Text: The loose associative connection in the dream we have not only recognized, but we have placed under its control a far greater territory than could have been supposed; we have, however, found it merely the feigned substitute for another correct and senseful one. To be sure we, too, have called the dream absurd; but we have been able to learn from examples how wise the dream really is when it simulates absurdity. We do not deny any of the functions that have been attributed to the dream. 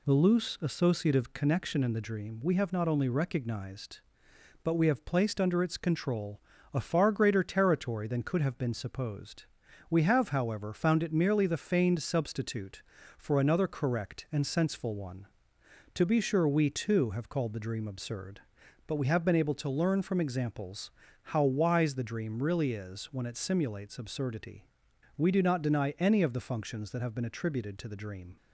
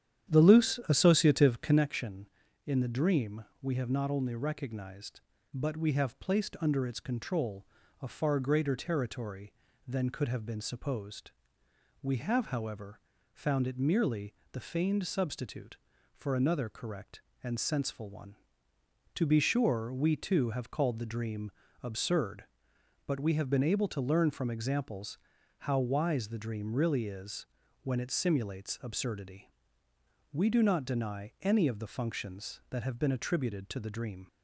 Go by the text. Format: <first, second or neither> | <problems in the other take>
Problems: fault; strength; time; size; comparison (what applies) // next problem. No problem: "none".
first | starts louder than the rest; strong; until 1.8 s; 10 dB // pauses between "dream" and "we"; slight; at 3.4 s; 0.16 s long // pauses between "control" and "a"; slight; at 7.6 s; 0.36 s long; slight in the first // pauses between "merely" and "the"; slight; at 14.3 s; 0.18 s long // pauses between "dream" and "absurd"; slight; at 21.4 s; 0.32 s long // pauses between "examples" and "how"; at 25.1 s; 0.44 s long; slight in the first // pauses between "is" and "when"; slight; at 27.4 s; 0.34 s long